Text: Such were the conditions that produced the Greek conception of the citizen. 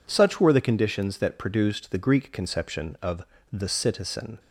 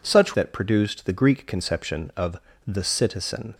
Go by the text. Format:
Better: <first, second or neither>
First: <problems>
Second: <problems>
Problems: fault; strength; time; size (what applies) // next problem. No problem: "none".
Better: first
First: pauses between "of" and "the"; slight; at 3.2 s; 0.28 s long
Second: skips "were the conditions"; at 0.3 s // pauses between "of" and "the"; slight; at 2.3 s; 0.28 s long